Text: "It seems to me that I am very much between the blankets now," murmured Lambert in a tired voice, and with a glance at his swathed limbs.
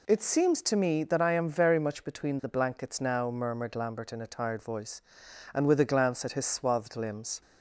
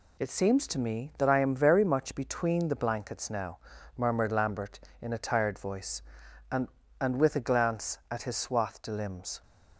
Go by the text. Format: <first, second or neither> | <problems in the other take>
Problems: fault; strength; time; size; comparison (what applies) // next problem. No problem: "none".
first | says "and" twice; at 7.0 s